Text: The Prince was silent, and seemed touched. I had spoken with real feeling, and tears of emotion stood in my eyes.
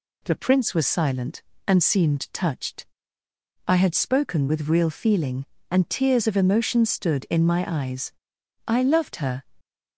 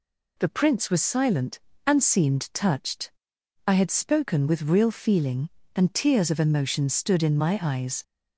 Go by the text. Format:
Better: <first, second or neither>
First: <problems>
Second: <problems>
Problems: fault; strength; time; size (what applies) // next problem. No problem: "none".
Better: second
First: goes on to say "I loved her"; noticeable; from 8.6 s on; 0.74 s long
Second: none